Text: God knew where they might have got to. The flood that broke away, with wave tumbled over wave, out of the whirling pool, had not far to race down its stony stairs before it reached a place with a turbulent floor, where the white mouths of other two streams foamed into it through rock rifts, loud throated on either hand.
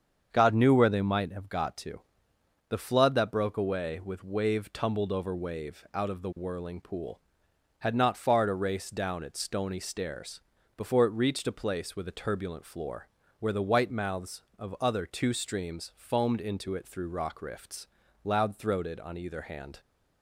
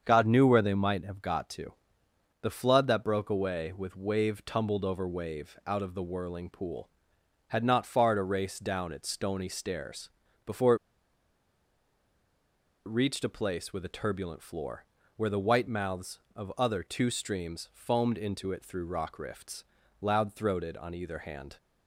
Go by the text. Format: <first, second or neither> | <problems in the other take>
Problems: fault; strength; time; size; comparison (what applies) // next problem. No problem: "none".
first | starts louder than the rest; until 1.0 s; 7 dB; also in the first // pauses between "stairs" and "before"; slight; at 10.0 s; 0.36 s long; slight in the first // pauses between "before" and "it"; strong; at 10.7 s; 2.1 s long